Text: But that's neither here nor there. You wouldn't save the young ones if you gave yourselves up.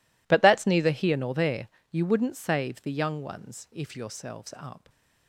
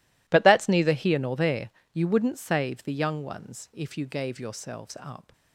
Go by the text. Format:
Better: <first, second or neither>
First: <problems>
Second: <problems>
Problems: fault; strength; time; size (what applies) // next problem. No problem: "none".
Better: second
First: skips "you gave"; at 3.9 s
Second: none